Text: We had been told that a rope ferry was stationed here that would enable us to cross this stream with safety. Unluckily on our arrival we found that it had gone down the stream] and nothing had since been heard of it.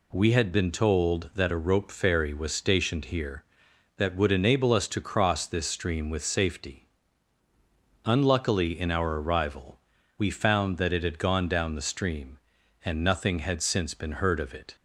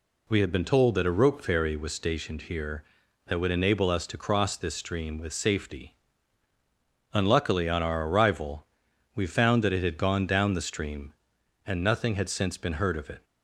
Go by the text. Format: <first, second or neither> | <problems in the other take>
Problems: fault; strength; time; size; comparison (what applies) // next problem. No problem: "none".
second | says "in" for "on"; at 8.7 s // pauses between "arrival" and "we"; at 9.7 s; 0.38 s long; noticeable in the second